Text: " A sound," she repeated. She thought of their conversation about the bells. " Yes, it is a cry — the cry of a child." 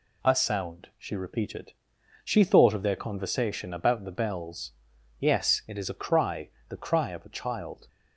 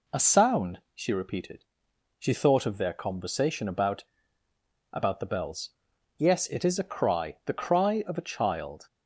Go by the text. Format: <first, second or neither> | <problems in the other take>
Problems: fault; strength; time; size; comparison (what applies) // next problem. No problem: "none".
first | says "about" twice; at 4.9 s